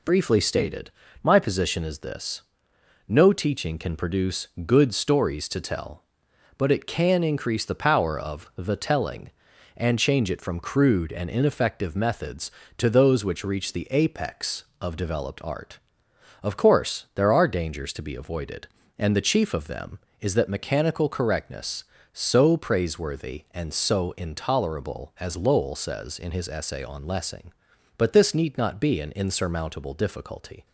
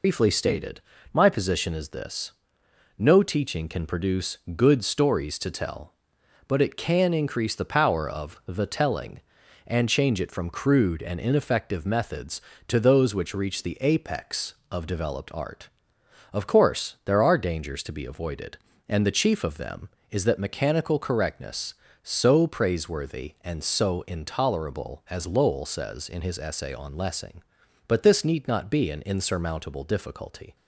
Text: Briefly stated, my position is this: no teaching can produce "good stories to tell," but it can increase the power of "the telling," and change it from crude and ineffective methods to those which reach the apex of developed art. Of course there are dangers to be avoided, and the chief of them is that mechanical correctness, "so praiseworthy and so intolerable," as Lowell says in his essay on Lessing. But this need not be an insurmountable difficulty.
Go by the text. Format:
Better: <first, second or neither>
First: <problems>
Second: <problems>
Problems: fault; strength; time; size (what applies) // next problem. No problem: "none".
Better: first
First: pauses between "produce" and "good"; slight; at 4.4 s; 0.20 s long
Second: loses the start of "Briefly"; at 0.0 s; 95 ms // pauses between "produce" and "good"; slight; at 4.3 s; 0.20 s long